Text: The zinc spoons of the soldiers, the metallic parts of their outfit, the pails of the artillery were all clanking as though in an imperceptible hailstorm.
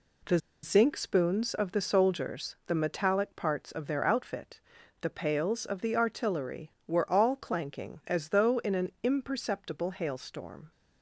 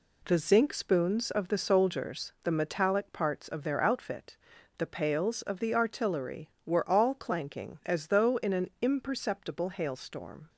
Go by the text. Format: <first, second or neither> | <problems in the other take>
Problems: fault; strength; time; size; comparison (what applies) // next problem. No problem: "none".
second | pauses between "The" and "zinc"; slight; at 0.3 s; 0.25 s long